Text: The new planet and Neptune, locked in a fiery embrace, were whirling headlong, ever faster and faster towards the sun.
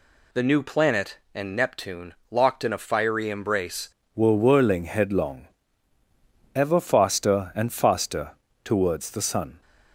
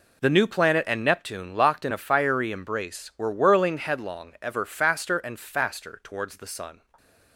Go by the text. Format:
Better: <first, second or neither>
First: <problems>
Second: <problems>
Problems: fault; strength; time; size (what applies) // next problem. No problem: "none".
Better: second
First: changes voice at "were"; from 4.1 s on; 5.5 s long // pauses between "faster" and "towards"; slight; at 8.3 s; 0.34 s long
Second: none